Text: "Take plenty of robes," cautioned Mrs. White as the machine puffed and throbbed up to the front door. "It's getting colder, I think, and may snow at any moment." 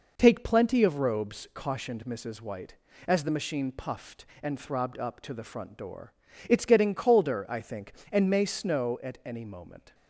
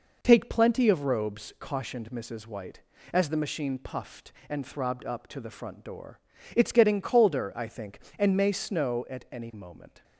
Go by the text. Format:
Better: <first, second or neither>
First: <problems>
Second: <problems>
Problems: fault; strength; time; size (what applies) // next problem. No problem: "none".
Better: neither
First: none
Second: none